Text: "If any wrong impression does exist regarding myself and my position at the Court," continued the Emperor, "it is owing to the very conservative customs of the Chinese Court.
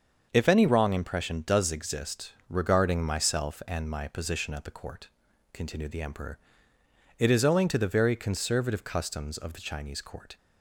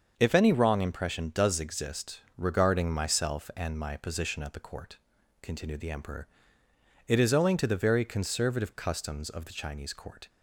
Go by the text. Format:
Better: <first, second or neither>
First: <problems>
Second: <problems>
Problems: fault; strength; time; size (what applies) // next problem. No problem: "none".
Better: neither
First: starts louder than the rest; until 1.3 s; 6.5 dB // pauses between "exist" and "regarding"; slight; at 2.3 s; 0.16 s long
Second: starts louder than the rest; until 1.1 s; 6.5 dB // pauses between "exist" and "regarding"; slight; at 2.2 s; 0.16 s long